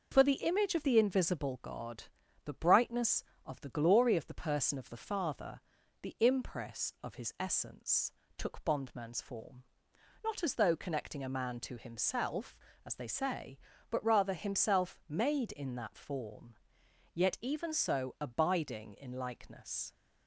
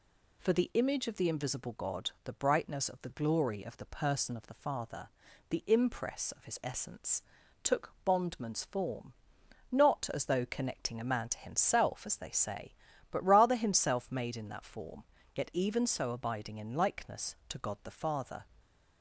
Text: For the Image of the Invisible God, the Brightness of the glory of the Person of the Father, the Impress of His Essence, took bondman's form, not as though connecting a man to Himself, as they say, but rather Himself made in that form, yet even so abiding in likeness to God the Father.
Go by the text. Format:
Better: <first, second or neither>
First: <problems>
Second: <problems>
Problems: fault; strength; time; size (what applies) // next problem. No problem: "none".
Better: second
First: stops before "to God the Father"; at 19.9 s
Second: none